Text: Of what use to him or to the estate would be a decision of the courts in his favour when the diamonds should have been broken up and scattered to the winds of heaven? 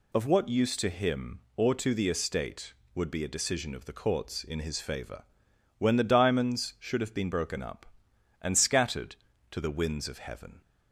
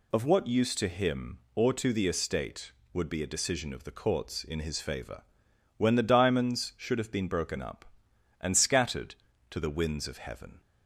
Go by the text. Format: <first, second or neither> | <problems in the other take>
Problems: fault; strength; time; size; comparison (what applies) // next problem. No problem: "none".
neither | pauses between "favour" and "when"; noticeable; the same in both